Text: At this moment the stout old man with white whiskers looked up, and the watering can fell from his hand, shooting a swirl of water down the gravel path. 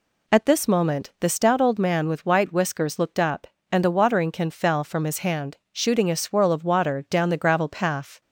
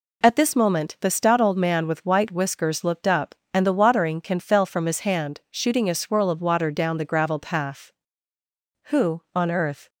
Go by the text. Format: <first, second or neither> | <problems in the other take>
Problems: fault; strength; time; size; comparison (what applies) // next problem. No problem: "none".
first | goes on to say "Who on earth"; noticeable; from 8.8 s on; 1.0 s long